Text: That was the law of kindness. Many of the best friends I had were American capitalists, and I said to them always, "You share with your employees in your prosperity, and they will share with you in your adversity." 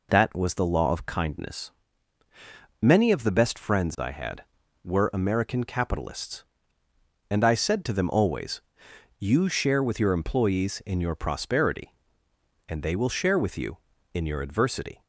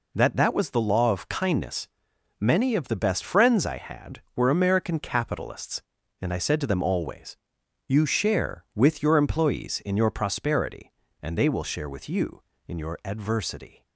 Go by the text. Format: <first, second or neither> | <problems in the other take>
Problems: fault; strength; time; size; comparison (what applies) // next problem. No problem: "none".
first | says "That" twice; at 0.3 s